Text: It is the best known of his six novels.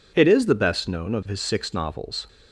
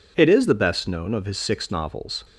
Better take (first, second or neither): neither